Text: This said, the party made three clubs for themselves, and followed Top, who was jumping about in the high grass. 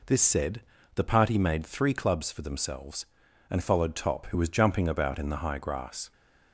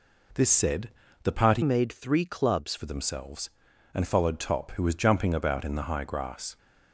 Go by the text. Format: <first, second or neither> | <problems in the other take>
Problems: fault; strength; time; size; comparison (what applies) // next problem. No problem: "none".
first | changes voice from "made" to "clubs"; from 1.6 to 2.7 s; 1.1 s long